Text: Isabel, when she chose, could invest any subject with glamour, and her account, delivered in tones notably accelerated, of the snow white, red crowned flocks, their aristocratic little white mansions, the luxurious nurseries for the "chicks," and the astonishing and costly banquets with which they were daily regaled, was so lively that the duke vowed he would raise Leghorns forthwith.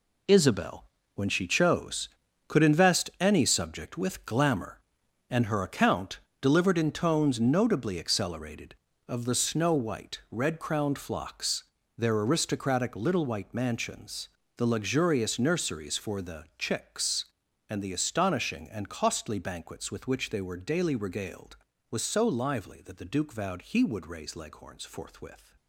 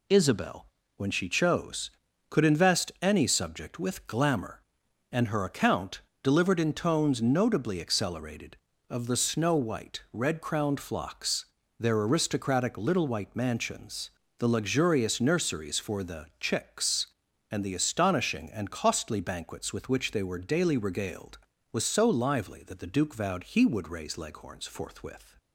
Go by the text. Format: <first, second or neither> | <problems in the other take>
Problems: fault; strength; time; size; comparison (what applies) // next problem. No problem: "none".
second | gets quieter; strong; throughout; 10 dB